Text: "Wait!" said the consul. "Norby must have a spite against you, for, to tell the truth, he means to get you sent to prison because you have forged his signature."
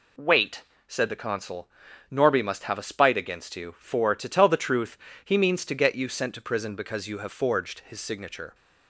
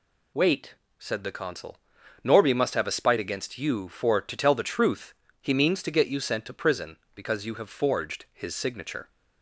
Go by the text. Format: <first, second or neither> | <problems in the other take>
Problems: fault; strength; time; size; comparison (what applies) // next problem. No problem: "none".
neither | none